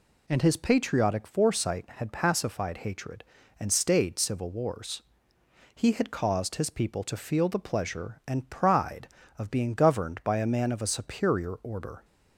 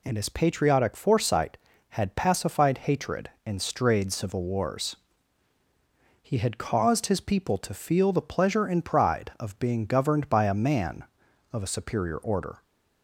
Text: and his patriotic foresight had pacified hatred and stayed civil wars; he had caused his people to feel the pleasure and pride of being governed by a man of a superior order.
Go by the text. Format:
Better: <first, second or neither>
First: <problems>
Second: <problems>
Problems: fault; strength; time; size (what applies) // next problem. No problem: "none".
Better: first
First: none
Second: says "strayed" for "stayed"; at 3.6 s